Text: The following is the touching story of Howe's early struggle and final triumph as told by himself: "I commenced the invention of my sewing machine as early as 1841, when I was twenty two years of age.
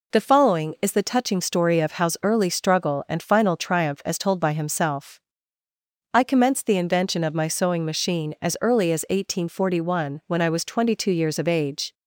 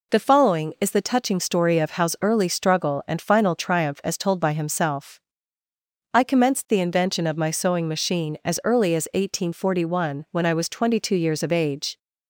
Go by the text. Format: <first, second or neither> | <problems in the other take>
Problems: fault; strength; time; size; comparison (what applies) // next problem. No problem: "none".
neither | none